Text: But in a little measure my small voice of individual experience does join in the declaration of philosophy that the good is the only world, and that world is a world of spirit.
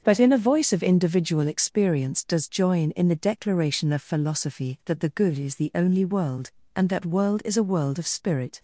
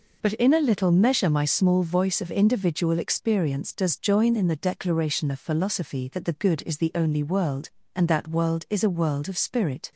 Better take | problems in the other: second | starts louder than the rest; until 1.0 s; 6.5 dB // skips "little measure my small"; at 0.3 s

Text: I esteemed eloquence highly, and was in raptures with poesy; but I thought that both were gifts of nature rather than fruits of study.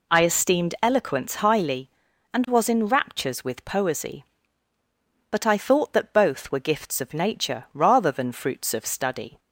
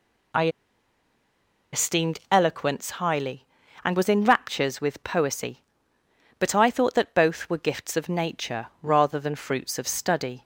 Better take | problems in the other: first | pauses between "I" and "esteemed"; at 0.4 s; 1.2 s long // pauses between "nature" and "rather"; slight; at 8.6 s; 0.16 s long

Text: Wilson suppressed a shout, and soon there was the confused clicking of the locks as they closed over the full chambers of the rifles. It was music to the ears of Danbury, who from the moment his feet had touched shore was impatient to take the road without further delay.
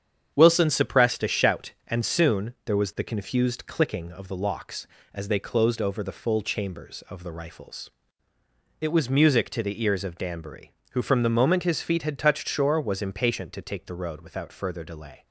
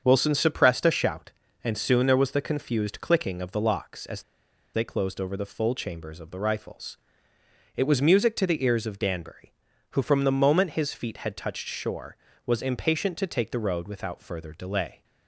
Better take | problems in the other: first | starts louder than the rest; until 1.0 s; 7 dB; strong in the first // pauses between "as" and "they"; noticeable; at 4.2 s; 0.51 s long

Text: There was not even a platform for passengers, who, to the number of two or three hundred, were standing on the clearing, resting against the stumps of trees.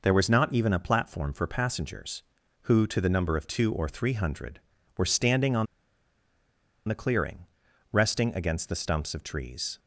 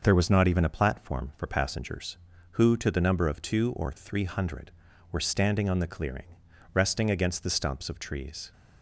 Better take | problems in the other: second | pauses between "on" and "the"; at 5.6 s; 1.2 s long

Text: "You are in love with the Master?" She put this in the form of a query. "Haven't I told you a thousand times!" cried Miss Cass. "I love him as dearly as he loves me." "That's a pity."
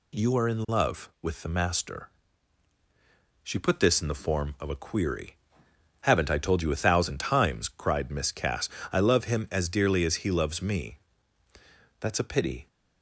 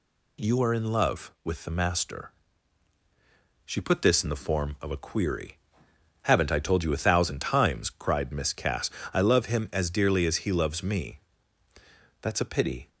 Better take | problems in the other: neither | none

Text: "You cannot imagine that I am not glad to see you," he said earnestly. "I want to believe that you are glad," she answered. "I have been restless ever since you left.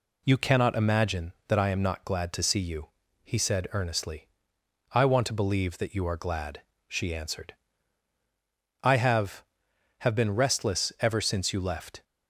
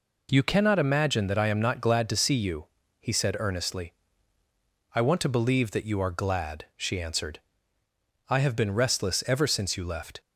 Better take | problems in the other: second | says "have" twice; at 9.9 s

